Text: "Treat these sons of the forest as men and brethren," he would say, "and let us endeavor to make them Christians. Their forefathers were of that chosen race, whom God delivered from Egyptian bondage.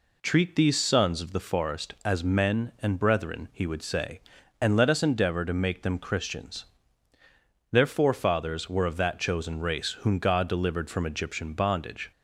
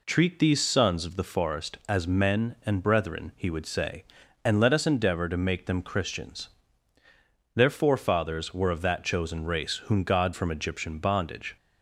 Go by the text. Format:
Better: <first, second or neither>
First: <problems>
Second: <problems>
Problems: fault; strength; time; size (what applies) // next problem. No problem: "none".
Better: first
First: none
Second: skips "delivered"; at 10.3 s